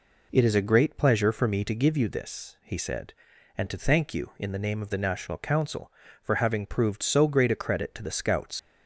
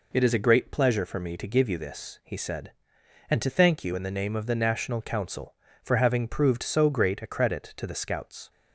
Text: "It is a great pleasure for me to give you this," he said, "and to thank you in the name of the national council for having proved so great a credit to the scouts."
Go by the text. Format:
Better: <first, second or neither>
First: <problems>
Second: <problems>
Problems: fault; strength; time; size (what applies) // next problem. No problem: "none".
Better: second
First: leaves "scouts" unfinished; at 8.5 s; 95 ms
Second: none